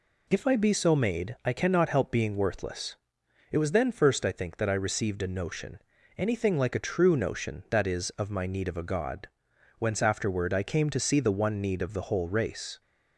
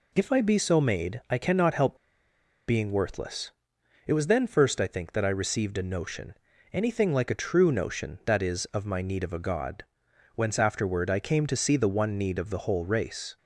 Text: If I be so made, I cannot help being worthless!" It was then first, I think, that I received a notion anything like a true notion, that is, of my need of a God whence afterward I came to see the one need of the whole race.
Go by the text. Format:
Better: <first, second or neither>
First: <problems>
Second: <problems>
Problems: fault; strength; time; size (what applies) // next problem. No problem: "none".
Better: first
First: pauses between "notion" and "anything"; at 5.7 s; 0.38 s long // pauses between "God" and "whence"; noticeable; at 9.2 s; 0.49 s long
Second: pauses between "help" and "being"; noticeable; at 1.9 s; 0.71 s long // pauses between "notion" and "anything"; at 6.3 s; 0.38 s long // pauses between "God" and "whence"; noticeable; at 9.8 s; 0.50 s long